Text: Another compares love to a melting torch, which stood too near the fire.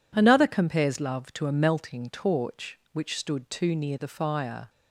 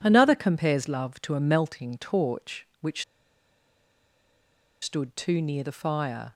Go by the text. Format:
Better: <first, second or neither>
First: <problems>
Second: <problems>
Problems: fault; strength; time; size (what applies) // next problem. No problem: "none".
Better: first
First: none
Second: pauses between "which" and "stood"; strong; at 3.0 s; 1.7 s long